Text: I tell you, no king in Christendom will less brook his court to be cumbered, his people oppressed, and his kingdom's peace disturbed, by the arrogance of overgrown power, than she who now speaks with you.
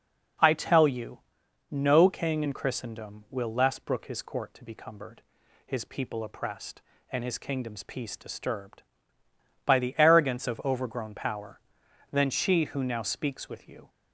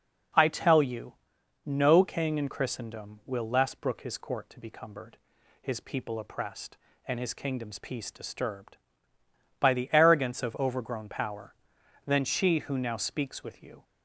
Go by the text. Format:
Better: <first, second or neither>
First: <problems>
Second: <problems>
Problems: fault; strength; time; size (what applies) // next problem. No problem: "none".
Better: neither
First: none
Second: none